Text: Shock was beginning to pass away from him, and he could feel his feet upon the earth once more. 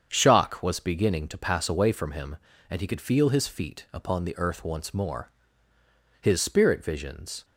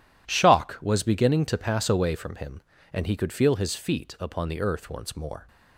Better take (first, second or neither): second